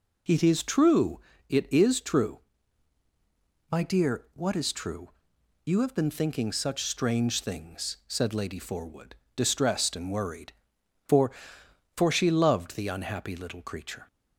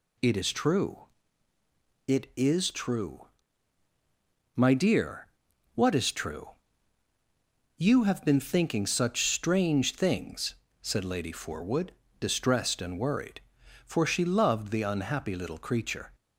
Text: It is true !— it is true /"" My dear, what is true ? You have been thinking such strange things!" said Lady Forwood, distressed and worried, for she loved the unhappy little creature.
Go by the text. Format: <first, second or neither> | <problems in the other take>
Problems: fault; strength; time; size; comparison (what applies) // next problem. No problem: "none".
second | says "for" twice; at 11.9 s